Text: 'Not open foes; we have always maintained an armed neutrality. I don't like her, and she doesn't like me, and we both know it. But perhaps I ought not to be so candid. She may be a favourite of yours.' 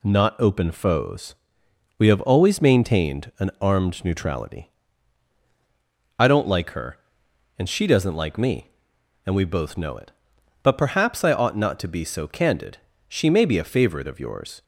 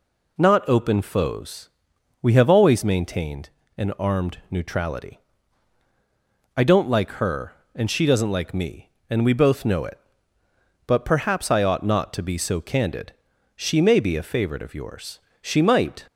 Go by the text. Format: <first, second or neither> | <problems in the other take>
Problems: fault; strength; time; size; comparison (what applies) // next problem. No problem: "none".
first | pauses between "maintained" and "an"; slight; at 3.4 s; 0.30 s long // goes on to say "She might"; noticeable; from 15.4 s on; 0.64 s long